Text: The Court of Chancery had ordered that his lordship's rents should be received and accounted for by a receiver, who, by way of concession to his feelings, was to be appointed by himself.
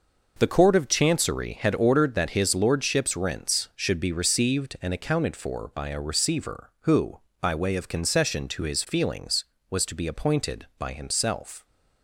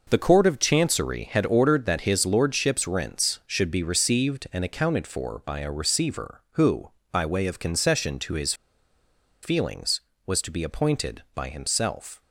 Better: first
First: none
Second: pauses between "his" and "feelings"; noticeable; at 8.5 s; 0.88 s long

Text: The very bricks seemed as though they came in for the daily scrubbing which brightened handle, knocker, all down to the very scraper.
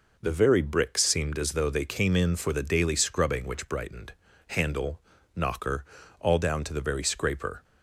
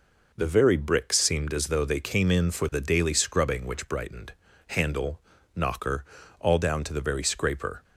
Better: neither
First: pauses between "brightened" and "handle"; slight; at 4.1 s; 0.34 s long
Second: pauses between "brightened" and "handle"; slight; at 4.3 s; 0.34 s long

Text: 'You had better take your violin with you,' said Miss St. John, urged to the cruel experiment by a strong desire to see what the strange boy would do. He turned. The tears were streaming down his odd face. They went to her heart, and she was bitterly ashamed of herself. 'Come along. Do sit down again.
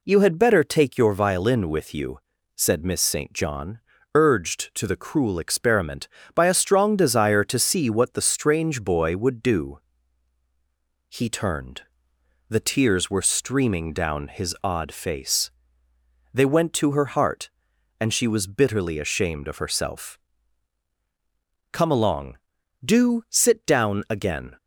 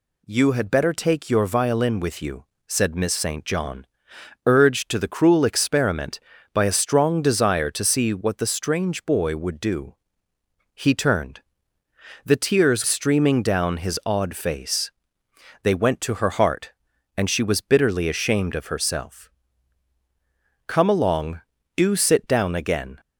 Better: first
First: none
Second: skips "were"; at 12.8 s

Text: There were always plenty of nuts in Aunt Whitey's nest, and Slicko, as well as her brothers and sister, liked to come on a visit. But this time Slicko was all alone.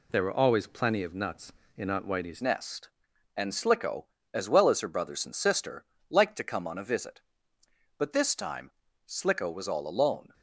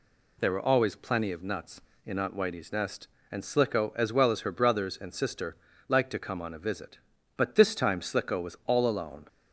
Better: second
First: changes voice at "nest"; from 2.4 s on; 7.9 s long // pauses between "time" and "Slicko"; slight; at 8.7 s; 0.36 s long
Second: none

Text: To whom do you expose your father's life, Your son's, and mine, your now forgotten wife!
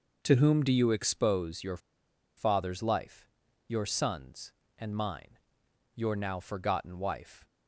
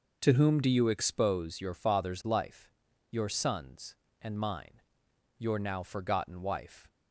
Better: second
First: pauses between "your" and "father's"; noticeable; at 1.7 s; 0.59 s long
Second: none

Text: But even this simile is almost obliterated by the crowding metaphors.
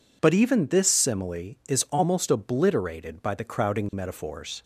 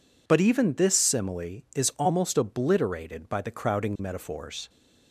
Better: neither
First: none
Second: none

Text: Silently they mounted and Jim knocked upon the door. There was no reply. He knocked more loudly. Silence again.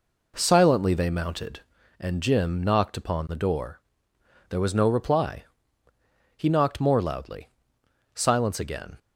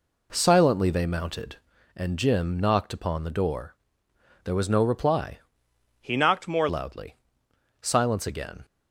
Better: first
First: none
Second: changes voice from "He" to "more"; from 6.0 to 6.6 s; 0.6 s long

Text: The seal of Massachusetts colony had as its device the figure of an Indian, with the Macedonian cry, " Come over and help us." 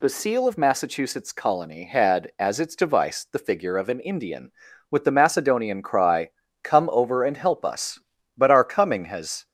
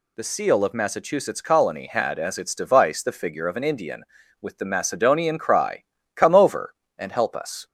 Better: second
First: goes on to say "But our coming has"; noticeable; from 8.3 s on; 1.0 s long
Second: none

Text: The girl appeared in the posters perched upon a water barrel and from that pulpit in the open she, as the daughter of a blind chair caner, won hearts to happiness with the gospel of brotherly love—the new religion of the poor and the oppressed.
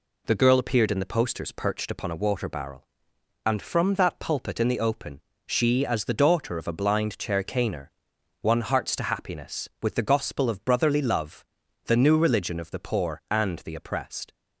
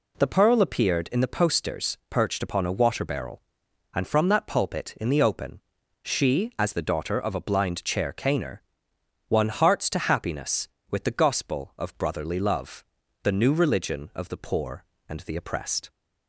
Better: first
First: pauses between "open" and "she"; slight; at 5.2 s; 0.26 s long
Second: says "pearl" for "girl"; at 0.2 s // pauses between "open" and "she"; at 5.5 s; 0.42 s long

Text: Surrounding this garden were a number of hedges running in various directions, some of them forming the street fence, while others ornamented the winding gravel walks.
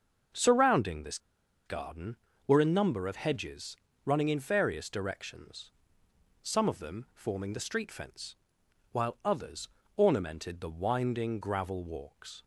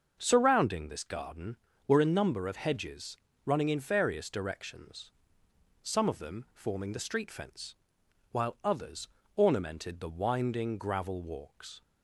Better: second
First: starts louder than the rest; until 1.8 s; 6.5 dB // pauses between "this" and "garden"; noticeable; at 1.1 s; 0.47 s long // pauses between "hedges" and "running"; slight; at 3.7 s; 0.30 s long // pauses between "others" and "ornamented"; slight; at 9.6 s; 0.26 s long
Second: starts louder than the rest; until 1.2 s; 6 dB // pauses between "hedges" and "running"; slight; at 3.1 s; 0.30 s long // pauses between "others" and "ornamented"; slight; at 9.0 s; 0.26 s long

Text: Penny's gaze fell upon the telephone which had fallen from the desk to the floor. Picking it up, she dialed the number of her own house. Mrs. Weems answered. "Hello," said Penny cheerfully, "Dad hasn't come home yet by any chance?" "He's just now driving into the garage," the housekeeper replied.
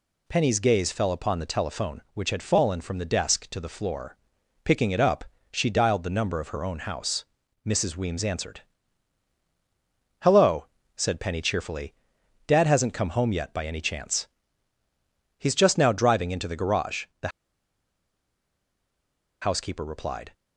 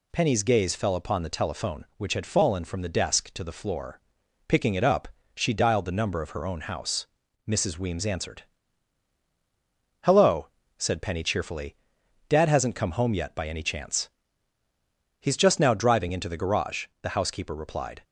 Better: second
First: pauses between "the" and "housekeeper"; strong; at 17.2 s; 2.1 s long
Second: none

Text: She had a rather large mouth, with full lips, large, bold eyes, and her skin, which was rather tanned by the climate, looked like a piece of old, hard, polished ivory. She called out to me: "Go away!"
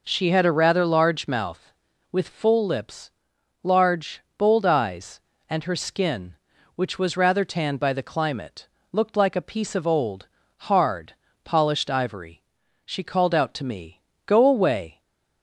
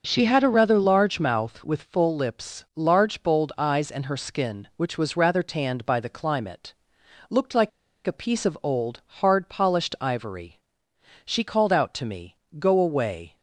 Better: first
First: none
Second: pauses between "like" and "a"; at 7.6 s; 0.36 s long

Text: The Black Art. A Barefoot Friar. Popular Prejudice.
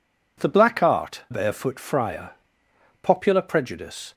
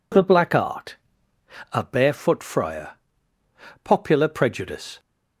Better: second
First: skips "A"; at 1.2 s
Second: none

